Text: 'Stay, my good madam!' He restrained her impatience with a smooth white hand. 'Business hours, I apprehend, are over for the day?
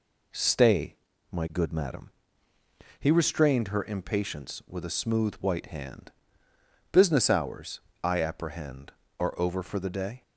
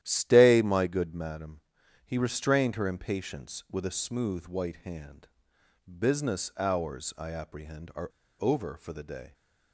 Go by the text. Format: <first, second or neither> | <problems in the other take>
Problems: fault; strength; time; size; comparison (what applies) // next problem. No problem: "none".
first | starts louder than the rest; strong; until 1.0 s; 12 dB // pauses between "are" and "over"; slight; at 8.0 s; 0.30 s long